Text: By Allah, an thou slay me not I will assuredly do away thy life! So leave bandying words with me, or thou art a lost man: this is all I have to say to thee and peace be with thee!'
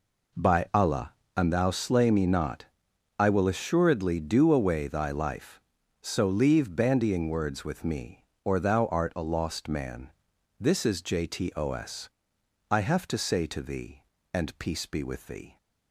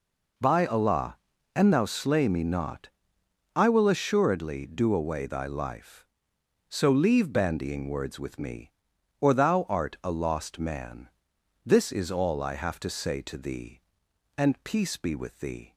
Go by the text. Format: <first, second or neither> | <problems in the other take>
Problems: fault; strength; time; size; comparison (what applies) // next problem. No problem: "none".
second | pauses between "not" and "I"; noticeable; at 2.6 s; 0.54 s long; noticeable in the second // says "jtos" for "all"; at 11.0 s